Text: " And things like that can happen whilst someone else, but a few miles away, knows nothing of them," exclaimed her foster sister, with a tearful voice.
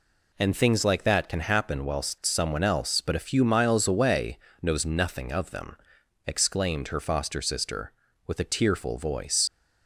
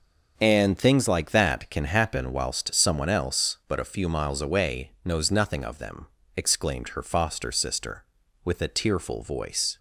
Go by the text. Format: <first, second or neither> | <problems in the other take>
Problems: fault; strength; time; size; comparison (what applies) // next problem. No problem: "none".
second | leaves "voice" unfinished; at 9.4 s; 90 ms